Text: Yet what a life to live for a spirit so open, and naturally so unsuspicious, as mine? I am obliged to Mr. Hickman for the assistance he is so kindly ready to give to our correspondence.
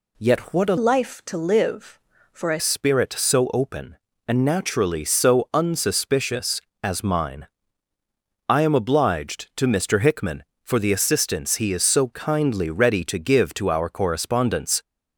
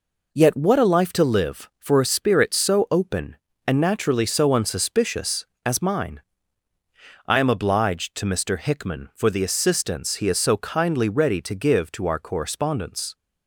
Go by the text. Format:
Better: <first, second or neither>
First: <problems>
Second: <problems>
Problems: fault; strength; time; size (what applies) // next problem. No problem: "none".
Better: second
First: changes voice from "life" to "a"; from 0.7 to 2.5 s; 1.8 s long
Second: none